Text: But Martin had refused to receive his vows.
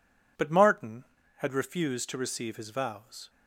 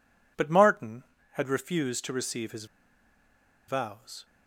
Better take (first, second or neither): first